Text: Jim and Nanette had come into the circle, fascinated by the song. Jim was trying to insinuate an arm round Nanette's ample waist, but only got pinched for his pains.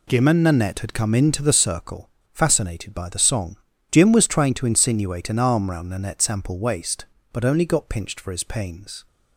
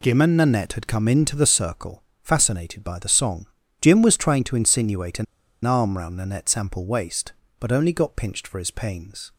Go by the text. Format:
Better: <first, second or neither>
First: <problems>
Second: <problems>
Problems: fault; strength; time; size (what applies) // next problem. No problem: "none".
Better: first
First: none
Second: pauses between "an" and "arm"; at 5.2 s; 0.40 s long